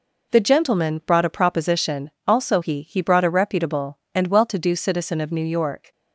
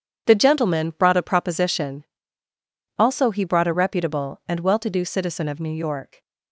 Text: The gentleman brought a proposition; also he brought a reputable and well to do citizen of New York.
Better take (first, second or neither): second